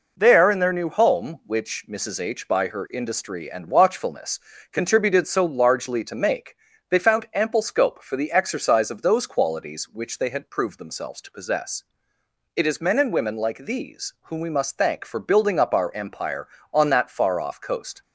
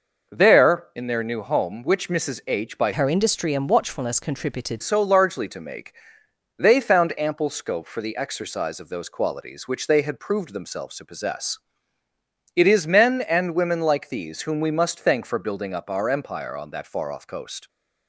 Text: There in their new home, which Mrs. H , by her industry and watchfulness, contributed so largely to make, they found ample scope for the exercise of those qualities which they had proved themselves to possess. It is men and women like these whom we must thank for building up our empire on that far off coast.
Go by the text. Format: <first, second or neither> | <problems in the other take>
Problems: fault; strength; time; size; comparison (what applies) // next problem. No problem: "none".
first | changes voice from "her" to "contributed"; from 2.9 to 4.8 s; 1.9 s long